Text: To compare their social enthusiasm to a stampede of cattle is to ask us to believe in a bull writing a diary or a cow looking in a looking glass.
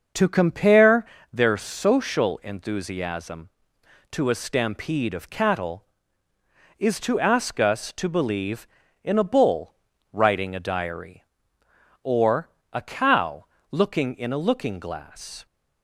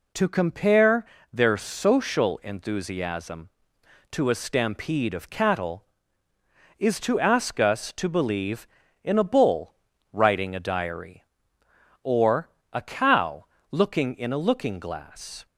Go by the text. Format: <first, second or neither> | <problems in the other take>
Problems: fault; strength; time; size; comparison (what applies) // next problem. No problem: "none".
second | starts louder than the rest; noticeable; until 1.4 s; 6 dB // pauses between "compare" and "their"; slight; at 1.0 s; 0.26 s long; slight in the second // pauses between "bull" and "writing"; slight; at 9.7 s; 0.36 s long; slight in the second // pauses between "or" and "a"; slight; at 12.4 s; 0.24 s long; slight in the second // pauses between "cow" and "looking"; slight; at 13.4 s; 0.24 s long; slight in the second